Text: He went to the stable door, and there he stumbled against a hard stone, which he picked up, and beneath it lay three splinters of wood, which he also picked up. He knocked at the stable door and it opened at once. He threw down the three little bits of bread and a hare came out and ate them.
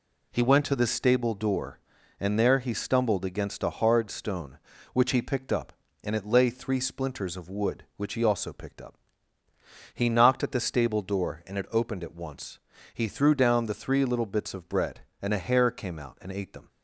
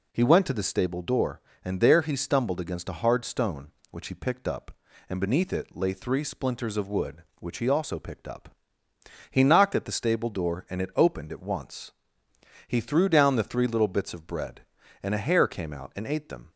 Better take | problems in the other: second | skips "beneath"; at 6.1 s

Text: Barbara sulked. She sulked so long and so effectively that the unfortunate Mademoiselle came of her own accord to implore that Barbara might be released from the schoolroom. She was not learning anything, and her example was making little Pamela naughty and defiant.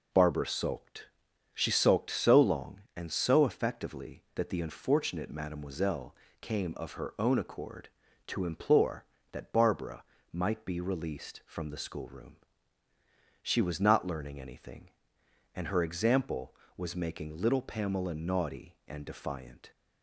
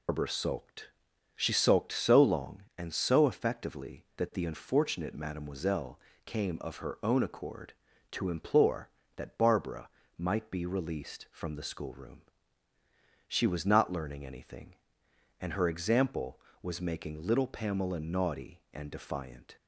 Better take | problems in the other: first | loses the start of "Barbara"; at 0.0 s; 135 ms // pauses between "Mademoiselle" and "came"; slight; at 5.9 s; 0.28 s long; slight in the first // pauses between "Barbara" and "might"; slight; at 9.8 s; 0.30 s long; slight in the first

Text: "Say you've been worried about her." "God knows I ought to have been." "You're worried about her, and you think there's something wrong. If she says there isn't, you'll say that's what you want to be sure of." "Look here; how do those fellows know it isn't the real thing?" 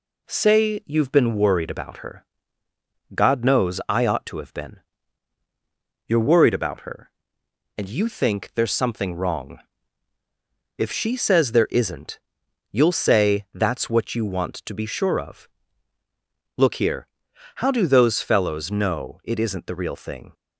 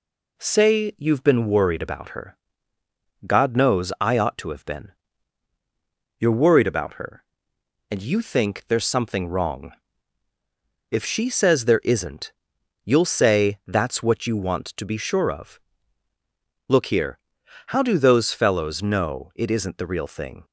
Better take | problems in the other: neither | none

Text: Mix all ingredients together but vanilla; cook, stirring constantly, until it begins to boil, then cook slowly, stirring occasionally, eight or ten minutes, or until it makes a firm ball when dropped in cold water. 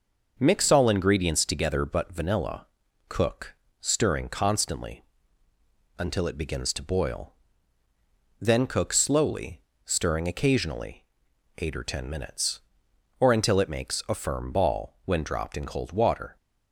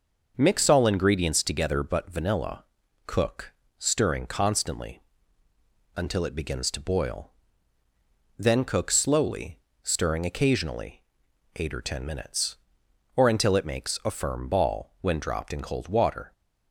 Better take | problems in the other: neither | none

